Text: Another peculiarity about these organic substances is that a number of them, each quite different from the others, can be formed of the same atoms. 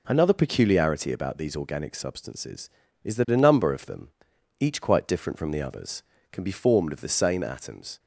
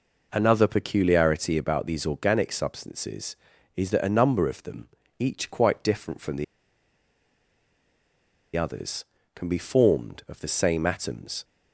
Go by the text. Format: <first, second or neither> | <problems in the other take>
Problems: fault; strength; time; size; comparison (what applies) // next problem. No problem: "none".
first | pauses between "the" and "others"; strong; at 6.4 s; 2.1 s long